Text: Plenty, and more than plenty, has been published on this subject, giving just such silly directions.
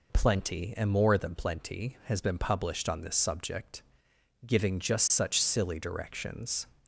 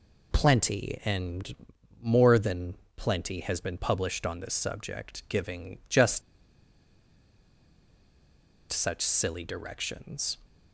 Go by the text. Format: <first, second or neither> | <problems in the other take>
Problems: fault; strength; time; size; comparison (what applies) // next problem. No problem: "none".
first | pauses between "and" and "more"; noticeable; at 1.5 s; 0.48 s long // pauses between "than" and "plenty"; slight; at 2.7 s; 0.22 s long // pauses between "just" and "such"; strong; at 6.2 s; 2.5 s long